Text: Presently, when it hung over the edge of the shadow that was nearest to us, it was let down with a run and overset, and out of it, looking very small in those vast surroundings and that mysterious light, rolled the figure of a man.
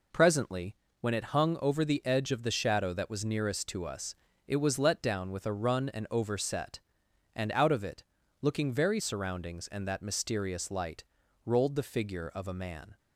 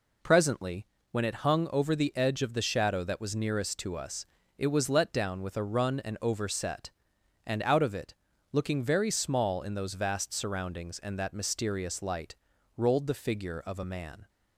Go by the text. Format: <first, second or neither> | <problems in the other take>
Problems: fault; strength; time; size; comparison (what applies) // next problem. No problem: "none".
second | skips "small in those vast"; at 9.0 s